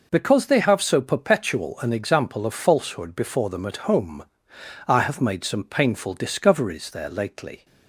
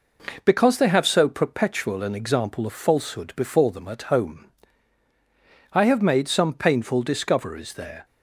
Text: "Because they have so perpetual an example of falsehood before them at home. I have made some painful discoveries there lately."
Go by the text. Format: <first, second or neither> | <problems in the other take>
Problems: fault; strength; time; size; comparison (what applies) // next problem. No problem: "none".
first | stops before "lately"; at 8.0 s